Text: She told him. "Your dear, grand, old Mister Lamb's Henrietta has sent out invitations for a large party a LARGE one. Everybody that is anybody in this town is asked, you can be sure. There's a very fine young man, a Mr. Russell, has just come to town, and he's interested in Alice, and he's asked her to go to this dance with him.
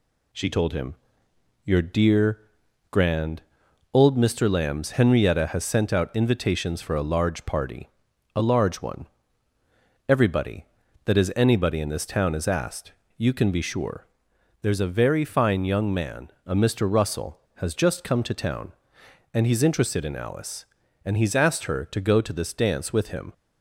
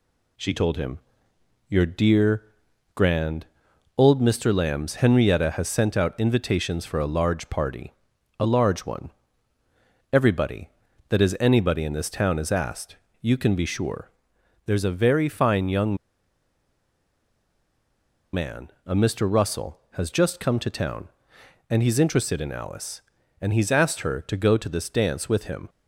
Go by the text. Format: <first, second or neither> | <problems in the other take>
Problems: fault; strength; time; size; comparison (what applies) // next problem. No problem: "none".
first | pauses between "party" and "a"; noticeable; at 7.9 s; 0.46 s long; noticeable in the first // pauses between "young" and "man"; strong; at 15.9 s; 2.3 s long